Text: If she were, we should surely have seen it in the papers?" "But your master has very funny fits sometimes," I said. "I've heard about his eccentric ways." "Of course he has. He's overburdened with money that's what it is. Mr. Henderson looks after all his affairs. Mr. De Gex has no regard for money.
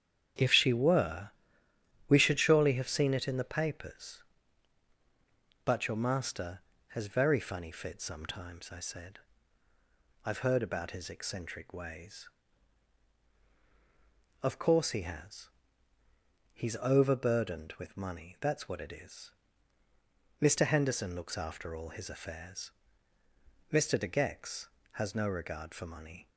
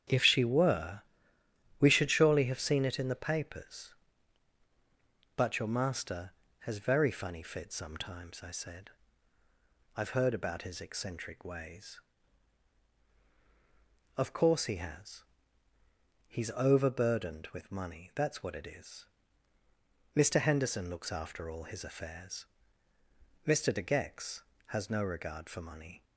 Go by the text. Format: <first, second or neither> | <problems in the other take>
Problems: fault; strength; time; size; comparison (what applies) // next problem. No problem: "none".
neither | starts louder than the rest; strong; the same in both